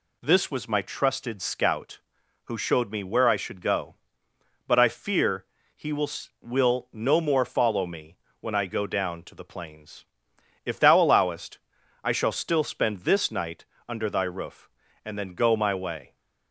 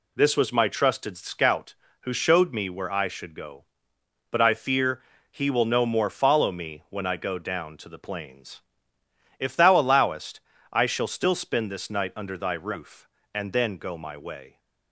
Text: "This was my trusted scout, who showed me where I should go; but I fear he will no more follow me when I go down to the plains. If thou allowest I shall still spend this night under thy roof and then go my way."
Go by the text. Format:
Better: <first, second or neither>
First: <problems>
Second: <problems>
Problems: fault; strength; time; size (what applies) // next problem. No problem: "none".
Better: second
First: pauses between "fear" and "he"; slight; at 5.4 s; 0.30 s long // says "will" twice; at 6.4 s // pauses between "me" and "when"; slight; at 8.1 s; 0.22 s long // pauses between "allowest" and "I"; at 11.5 s; 0.44 s long // pauses between "night" and "under"; slight; at 13.6 s; 0.22 s long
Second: pauses between "fear" and "he"; slight; at 5.0 s; 0.30 s long // pauses between "allowest" and "I"; slight; at 10.4 s; 0.32 s long